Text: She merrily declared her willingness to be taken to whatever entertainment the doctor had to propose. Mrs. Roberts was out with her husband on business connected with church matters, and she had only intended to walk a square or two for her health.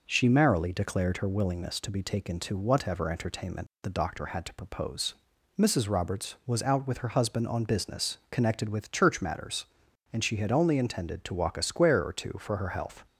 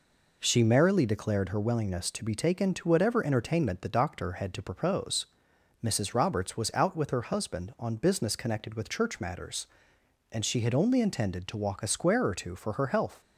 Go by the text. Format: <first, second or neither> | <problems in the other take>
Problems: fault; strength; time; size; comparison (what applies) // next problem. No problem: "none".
neither | none